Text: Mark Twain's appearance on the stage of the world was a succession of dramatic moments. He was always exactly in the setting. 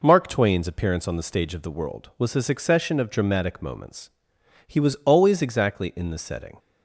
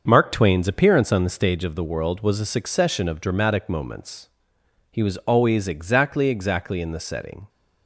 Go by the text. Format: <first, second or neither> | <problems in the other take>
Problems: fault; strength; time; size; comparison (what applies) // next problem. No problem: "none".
first | starts louder than the rest; until 1.0 s; 6.5 dB // says "exactly" twice; at 6.2 s